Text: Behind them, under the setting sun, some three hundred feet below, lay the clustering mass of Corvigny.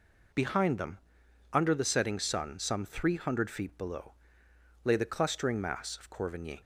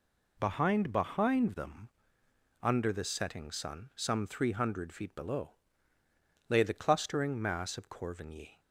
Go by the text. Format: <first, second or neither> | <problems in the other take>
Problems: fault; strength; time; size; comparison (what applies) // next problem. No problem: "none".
first | says "Behind" twice; at 0.9 s